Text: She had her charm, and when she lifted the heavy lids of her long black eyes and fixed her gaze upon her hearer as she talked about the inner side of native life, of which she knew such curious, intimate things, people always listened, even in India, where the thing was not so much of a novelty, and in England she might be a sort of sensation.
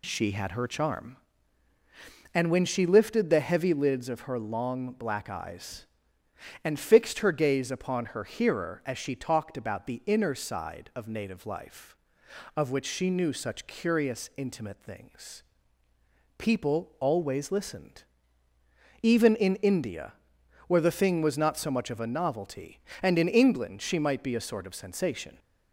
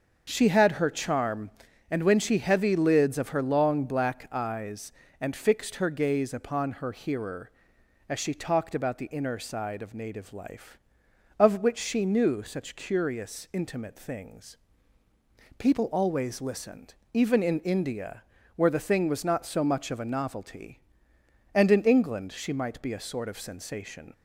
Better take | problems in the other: first | starts louder than the rest; until 1.3 s; 6.5 dB // skips "lifted the"; at 2.3 s

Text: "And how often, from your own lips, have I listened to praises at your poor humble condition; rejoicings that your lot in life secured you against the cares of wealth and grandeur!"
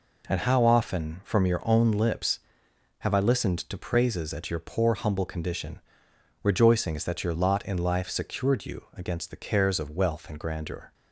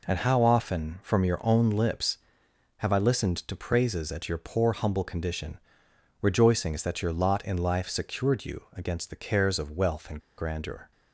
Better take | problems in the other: first | pauses between "and" and "grandeur"; slight; at 10.2 s; 0.17 s long

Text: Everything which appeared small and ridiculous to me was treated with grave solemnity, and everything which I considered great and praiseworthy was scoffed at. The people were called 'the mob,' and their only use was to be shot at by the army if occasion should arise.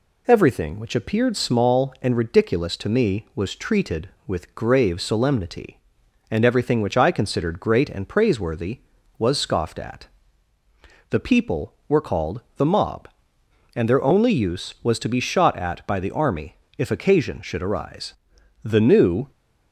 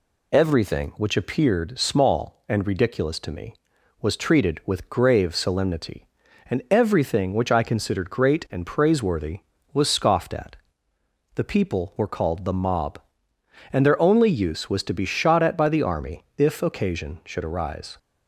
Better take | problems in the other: second | pauses between "army" and "if"; slight; at 16.5 s; 0.22 s long // goes on to say "The new"; noticeable; from 18.6 s on; 0.68 s long

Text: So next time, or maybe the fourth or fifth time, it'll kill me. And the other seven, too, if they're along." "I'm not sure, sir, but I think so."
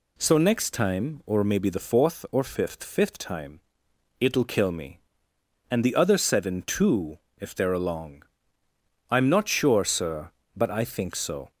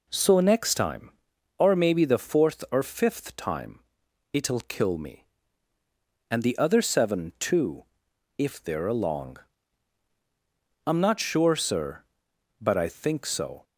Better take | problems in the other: second | says "fifth" twice; at 2.8 s

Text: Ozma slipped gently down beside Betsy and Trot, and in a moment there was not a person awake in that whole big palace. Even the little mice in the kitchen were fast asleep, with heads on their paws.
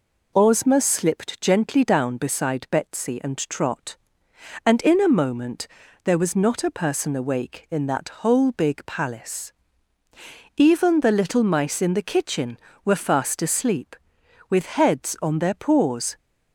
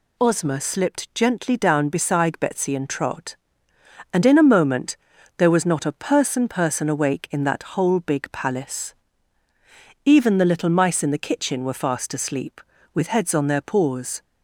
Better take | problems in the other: first | pauses between "moment" and "there"; at 4.9 s; 0.40 s long; also in the first // says "person" twice; at 6.4 s

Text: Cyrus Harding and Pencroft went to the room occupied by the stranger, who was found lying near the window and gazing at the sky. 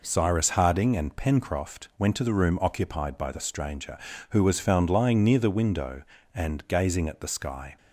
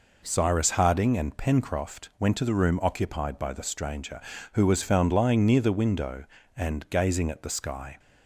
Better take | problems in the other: neither | none

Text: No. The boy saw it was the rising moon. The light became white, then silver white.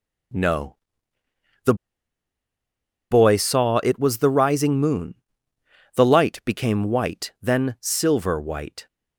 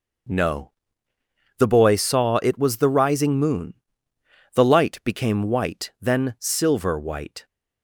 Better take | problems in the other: second | starts louder than the rest; noticeable; until 3.6 s; 6 dB // pauses between "The" and "boy"; strong; at 1.7 s; 1.3 s long

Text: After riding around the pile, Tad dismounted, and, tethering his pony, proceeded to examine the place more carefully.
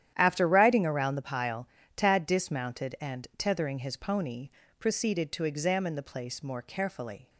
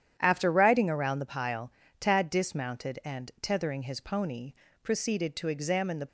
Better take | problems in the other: first | starts louder than the rest; strong; until 1.1 s; 9.5 dB; strong in the first // stops before "place more carefully"; at 6.0 s

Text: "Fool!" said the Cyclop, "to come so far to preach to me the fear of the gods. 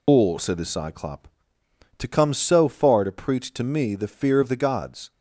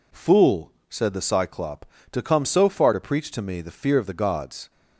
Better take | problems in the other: second | loses the start of "Fool"; at 0.0 s; 150 ms

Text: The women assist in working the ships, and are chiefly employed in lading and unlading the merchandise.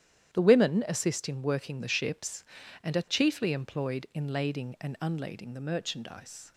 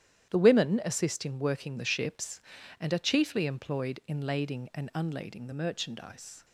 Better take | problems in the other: neither | starts louder than the rest; strong; the same in both

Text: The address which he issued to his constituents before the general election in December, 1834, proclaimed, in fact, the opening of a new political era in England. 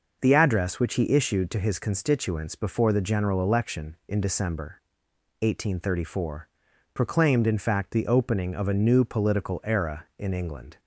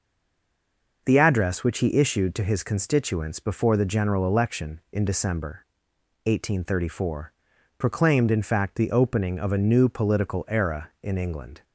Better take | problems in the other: first | stays silent before the first word; until 1.0 s; 1.0 s long

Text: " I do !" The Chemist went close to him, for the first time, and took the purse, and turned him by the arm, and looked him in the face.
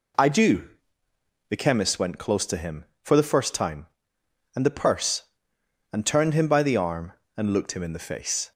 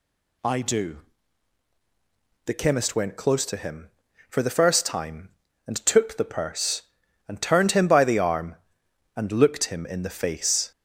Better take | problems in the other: second | skips "took"; at 4.6 s

